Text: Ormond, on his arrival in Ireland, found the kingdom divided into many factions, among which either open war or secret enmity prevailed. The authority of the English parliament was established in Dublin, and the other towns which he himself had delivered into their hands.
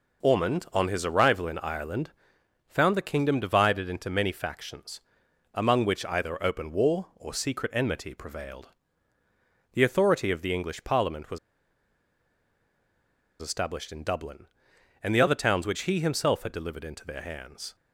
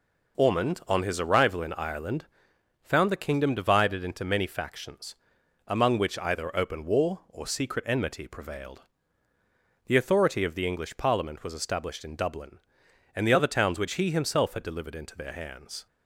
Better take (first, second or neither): second